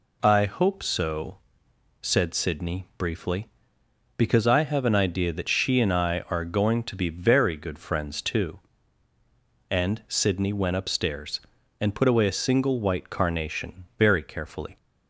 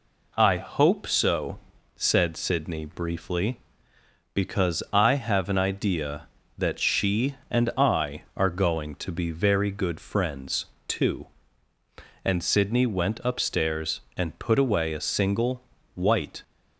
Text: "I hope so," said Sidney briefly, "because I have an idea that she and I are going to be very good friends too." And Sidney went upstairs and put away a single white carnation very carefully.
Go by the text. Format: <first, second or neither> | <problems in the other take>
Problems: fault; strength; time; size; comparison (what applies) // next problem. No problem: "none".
first | pauses between "friends" and "too"; slight; at 10.6 s; 0.22 s long // pauses between "single" and "white"; slight; at 15.6 s; 0.32 s long // stops before "carnation very carefully"; at 16.4 s